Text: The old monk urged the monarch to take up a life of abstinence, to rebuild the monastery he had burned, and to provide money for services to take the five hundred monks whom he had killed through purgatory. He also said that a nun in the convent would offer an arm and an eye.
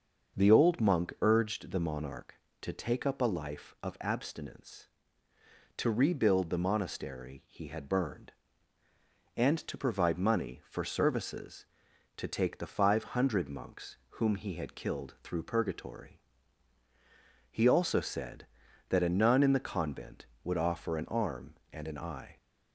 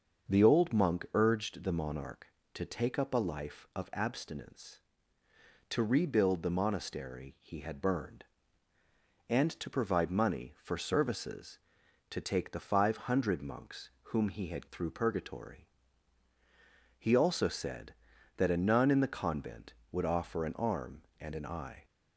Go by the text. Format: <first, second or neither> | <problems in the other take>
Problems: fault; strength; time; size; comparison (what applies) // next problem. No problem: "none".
first | starts louder than the rest; until 1.3 s; 6.5 dB; also in the first // skips "killed"; at 14.6 s